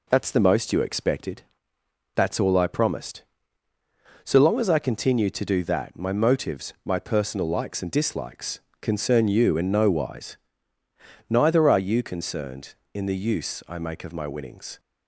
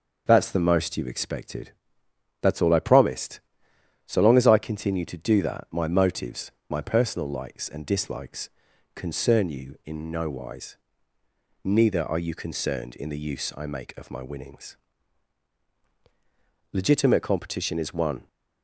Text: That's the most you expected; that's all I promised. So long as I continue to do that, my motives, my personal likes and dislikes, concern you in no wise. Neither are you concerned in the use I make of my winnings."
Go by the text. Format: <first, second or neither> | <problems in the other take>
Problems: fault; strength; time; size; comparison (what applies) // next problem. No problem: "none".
first | starts louder than the rest; until 1.2 s; 6 dB // goes on to say "Legitimate competition is one"; from 16.7 s on; 1.5 s long